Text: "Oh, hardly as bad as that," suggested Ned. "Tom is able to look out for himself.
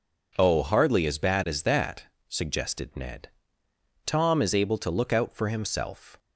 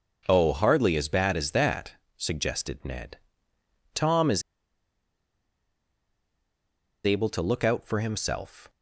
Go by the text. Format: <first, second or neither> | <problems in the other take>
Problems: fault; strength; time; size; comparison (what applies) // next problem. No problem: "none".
first | pauses between "is" and "able"; strong; at 4.4 s; 2.6 s long